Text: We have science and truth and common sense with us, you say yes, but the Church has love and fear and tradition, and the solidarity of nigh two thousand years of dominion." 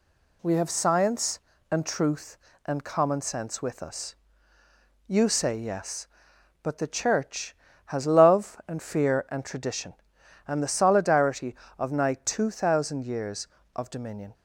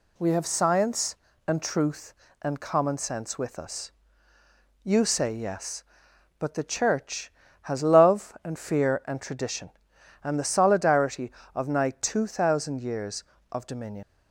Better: first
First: none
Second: leaves "dominion" unfinished; at 14.0 s; 65 ms

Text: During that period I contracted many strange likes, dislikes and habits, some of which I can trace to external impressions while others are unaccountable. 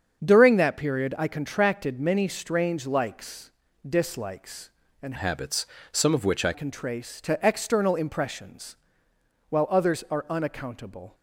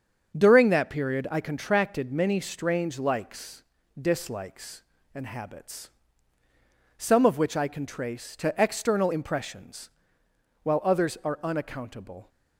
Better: second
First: starts louder than the rest; strong; until 1.2 s; 7 dB // changes voice from "habits" to "I"; from 5.1 to 6.5 s; 1.4 s long // pauses between "impressions" and "while"; noticeable; at 8.7 s; 0.72 s long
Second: starts louder than the rest; until 1.4 s; 6.5 dB // pauses between "impressions" and "while"; noticeable; at 9.9 s; 0.72 s long

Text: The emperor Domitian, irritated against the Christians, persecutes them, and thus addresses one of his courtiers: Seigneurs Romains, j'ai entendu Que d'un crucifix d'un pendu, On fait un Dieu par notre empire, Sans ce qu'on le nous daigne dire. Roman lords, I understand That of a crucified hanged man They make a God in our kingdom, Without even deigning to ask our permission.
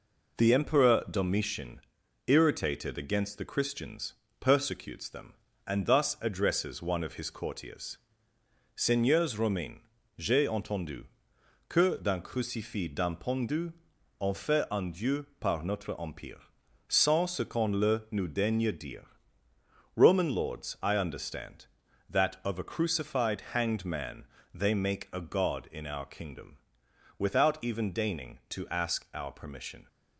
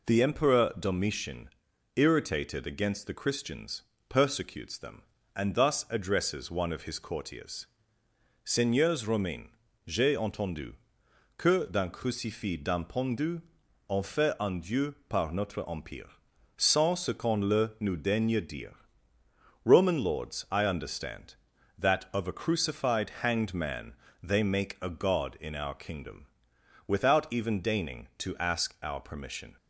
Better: second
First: gets quieter; noticeable; throughout; 4 dB // pauses between "entendu" and "Que"; noticeable; at 11.0 s; 0.64 s long // pauses between "man" and "They"; slight; at 24.2 s; 0.28 s long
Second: pauses between "entendu" and "Que"; noticeable; at 10.7 s; 0.64 s long // pauses between "man" and "They"; slight; at 23.9 s; 0.28 s long

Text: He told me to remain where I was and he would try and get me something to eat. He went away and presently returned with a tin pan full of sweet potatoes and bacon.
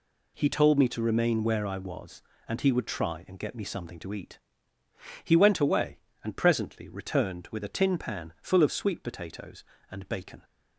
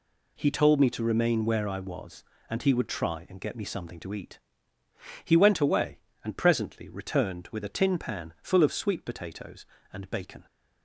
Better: neither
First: none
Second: none

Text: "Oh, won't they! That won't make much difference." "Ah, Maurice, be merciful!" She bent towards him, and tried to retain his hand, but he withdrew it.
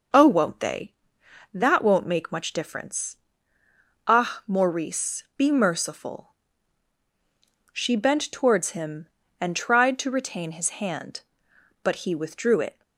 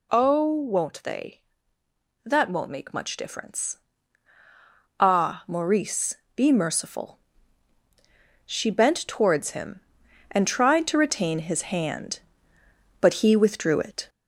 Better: first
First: none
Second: gets louder; slight; throughout; 2 dB

